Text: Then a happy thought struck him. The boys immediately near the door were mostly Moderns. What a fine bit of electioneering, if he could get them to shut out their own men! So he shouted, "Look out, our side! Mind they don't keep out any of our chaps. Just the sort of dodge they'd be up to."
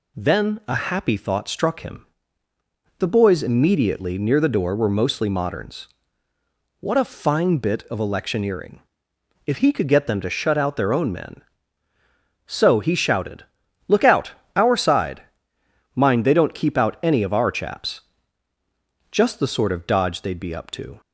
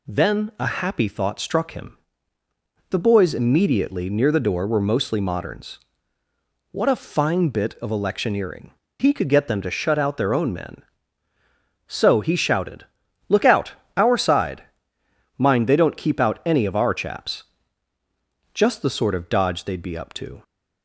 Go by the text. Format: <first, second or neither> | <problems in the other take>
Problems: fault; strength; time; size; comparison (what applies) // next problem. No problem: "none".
first | skips "if"; at 8.8 s